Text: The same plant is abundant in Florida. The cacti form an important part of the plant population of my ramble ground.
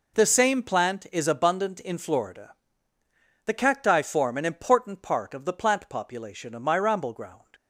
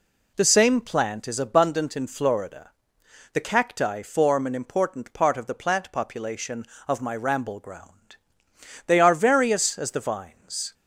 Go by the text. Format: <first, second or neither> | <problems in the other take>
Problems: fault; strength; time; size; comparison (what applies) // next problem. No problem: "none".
first | goes on to say "They are various as the vines"; strong; from 8.8 s on; 1.8 s long